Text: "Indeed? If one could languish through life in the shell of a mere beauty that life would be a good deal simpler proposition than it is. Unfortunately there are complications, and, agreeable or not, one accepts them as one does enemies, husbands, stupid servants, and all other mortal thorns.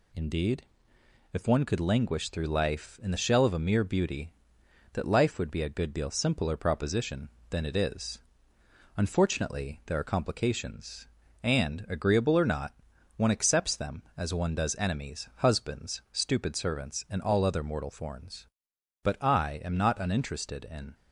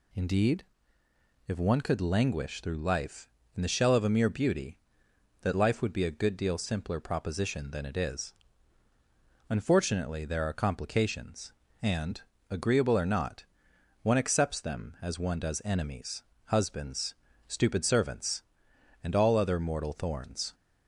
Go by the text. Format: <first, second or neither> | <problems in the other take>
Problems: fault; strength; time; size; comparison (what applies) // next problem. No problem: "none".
second | goes on to say "But I am not uninterested in"; strong; from 19.0 s on; 1.9 s long